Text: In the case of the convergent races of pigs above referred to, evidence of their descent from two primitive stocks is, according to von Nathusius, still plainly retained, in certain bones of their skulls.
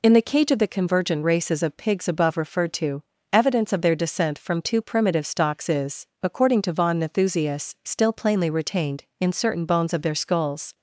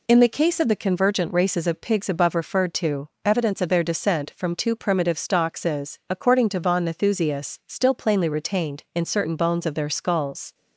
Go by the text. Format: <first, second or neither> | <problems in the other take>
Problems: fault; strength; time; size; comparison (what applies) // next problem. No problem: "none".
second | says "cage" for "case"; at 0.2 s